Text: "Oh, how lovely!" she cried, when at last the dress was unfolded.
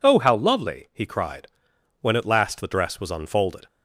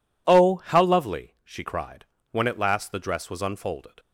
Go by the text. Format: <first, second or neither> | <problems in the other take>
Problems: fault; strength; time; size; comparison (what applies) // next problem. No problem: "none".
second | says "he" for "she"; at 0.9 s